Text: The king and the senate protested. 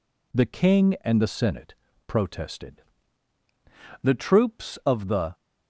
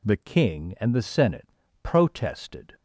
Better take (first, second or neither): second